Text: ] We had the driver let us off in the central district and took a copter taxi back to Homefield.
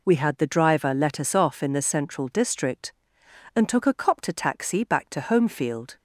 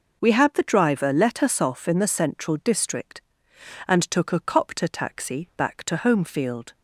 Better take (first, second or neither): neither